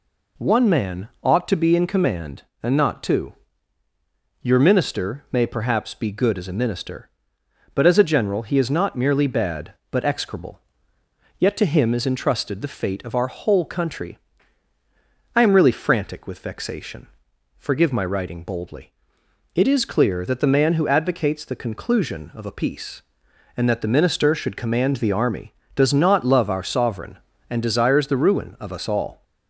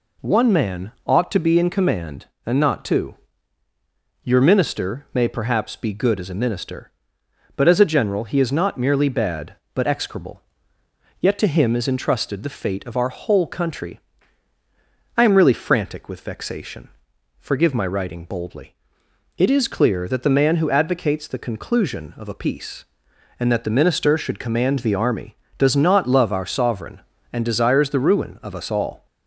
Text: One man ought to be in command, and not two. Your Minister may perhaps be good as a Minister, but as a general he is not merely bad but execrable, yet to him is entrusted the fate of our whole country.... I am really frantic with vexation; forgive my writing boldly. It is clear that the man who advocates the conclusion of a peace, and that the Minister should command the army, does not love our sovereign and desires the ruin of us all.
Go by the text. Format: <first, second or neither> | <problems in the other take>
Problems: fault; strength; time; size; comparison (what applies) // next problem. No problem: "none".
neither | pauses between "man" and "ought"; slight; the same in both